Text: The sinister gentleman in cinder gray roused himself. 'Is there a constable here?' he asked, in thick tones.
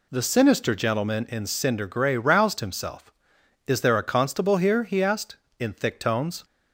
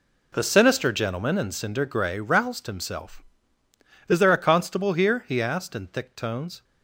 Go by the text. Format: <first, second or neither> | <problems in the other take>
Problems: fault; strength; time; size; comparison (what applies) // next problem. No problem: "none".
first | gets quieter; strong; throughout; 11.5 dB